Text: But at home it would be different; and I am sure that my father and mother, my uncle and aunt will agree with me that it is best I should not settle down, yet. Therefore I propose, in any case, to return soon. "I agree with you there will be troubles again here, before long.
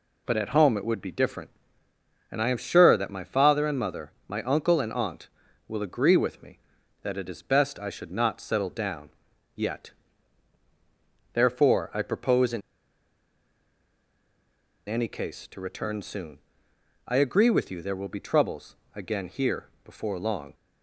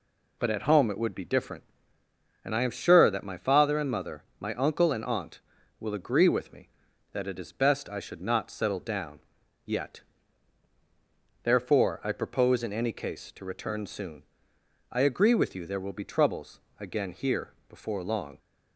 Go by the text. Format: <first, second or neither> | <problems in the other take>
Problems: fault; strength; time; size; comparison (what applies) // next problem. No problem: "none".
second | pauses between "in" and "any"; strong; at 12.6 s; 2.2 s long // pauses between "troubles" and "again"; slight; at 18.7 s; 0.22 s long; slight in the second